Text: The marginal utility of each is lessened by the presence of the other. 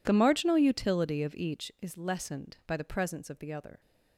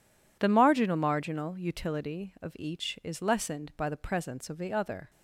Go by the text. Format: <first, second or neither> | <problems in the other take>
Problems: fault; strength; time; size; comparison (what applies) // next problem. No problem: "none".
first | says "marginal" twice; at 0.9 s